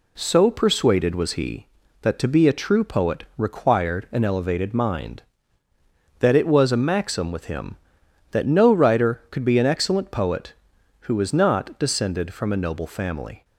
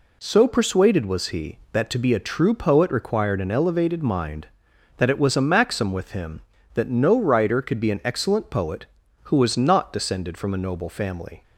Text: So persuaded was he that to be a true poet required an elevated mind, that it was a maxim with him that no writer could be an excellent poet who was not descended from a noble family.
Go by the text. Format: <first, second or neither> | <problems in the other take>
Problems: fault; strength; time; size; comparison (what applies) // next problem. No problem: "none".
neither | none